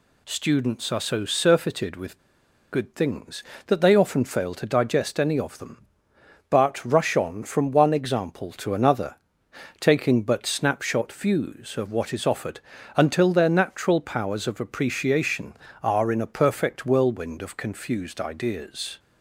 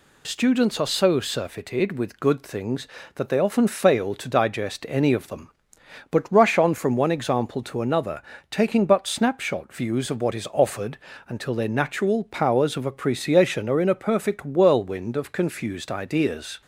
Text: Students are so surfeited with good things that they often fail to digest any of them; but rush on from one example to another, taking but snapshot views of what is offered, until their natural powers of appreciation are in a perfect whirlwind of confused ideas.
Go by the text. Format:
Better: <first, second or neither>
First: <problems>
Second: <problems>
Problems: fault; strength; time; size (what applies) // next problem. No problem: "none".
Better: second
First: pauses between "with" and "good"; noticeable; at 2.1 s; 0.53 s long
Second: none